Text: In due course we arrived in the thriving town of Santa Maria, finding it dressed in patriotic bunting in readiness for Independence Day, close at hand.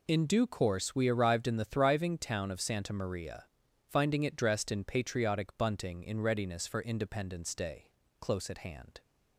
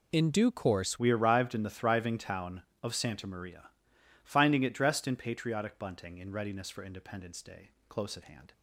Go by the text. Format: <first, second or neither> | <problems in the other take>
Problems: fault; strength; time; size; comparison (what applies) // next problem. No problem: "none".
first | changes voice at "we"; from 0.9 s on; 7.6 s long